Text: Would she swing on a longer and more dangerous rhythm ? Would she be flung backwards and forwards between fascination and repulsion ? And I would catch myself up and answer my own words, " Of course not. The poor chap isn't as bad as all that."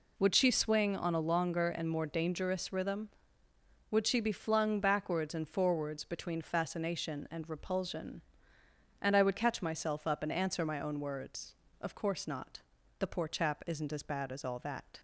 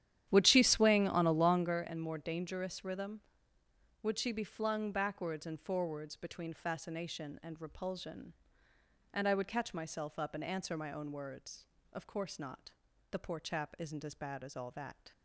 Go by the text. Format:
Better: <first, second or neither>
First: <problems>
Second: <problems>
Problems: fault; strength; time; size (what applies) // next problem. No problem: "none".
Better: first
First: none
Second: starts louder than the rest; strong; until 1.8 s; 11 dB